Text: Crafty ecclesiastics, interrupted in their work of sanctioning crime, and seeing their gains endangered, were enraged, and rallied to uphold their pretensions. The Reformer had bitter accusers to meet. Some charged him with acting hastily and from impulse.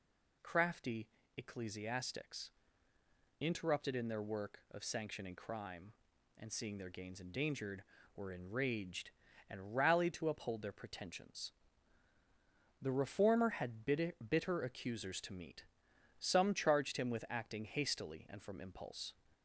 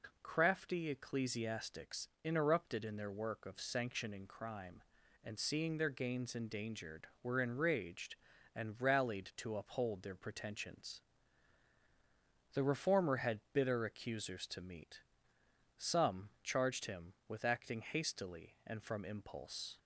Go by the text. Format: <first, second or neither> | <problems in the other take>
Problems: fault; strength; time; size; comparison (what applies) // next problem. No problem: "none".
second | pauses between "Crafty" and "ecclesiastics"; slight; at 1.0 s; 0.28 s long // says "bitter" twice; at 14.2 s